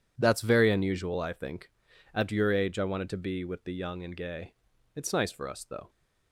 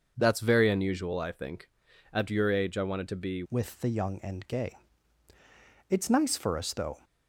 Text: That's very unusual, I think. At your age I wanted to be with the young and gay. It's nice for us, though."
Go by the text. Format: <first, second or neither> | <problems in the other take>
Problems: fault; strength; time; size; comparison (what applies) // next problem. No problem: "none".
first | changes voice at "with"; from 3.4 s on; 3.5 s long